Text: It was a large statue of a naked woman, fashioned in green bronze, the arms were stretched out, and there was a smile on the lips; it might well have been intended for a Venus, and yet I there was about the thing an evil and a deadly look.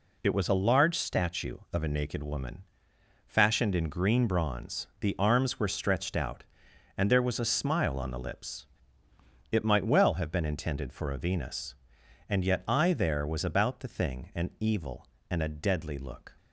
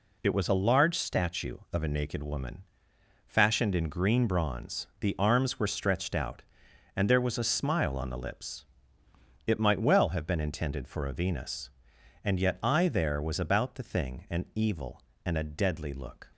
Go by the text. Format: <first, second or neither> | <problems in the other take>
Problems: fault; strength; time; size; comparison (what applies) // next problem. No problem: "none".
neither | none